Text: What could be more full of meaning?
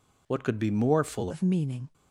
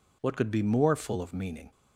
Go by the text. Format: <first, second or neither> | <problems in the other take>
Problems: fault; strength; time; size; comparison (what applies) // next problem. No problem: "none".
second | changes voice at "of"; from 1.2 s on; 0.6 s long